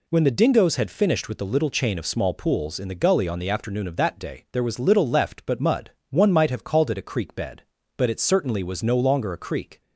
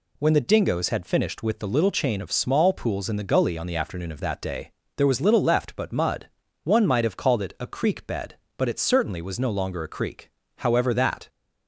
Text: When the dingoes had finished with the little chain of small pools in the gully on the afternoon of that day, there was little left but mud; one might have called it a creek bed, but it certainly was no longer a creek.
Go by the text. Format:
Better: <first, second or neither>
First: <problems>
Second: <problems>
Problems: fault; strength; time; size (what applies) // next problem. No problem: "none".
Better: first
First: none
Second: goes on to say "However that"; noticeable; from 10.5 s on; 0.72 s long